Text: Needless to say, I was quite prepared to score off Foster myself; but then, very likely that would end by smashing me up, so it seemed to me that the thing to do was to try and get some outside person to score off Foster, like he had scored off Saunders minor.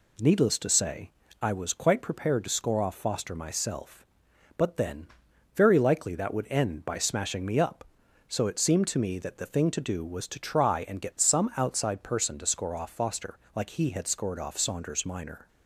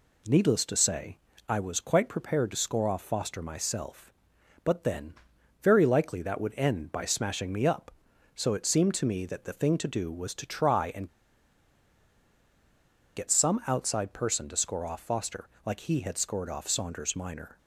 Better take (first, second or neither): first